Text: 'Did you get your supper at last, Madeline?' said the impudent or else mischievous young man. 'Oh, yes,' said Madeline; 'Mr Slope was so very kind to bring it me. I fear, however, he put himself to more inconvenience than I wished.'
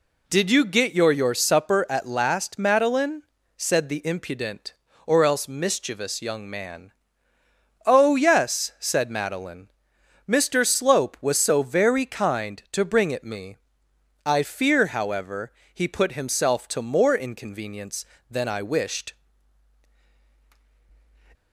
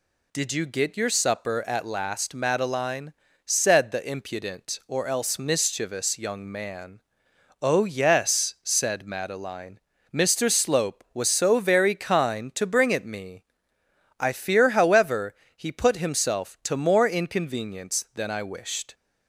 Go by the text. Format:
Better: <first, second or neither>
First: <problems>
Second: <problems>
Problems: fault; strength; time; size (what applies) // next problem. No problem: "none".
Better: second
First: says "your" twice; at 1.1 s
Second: none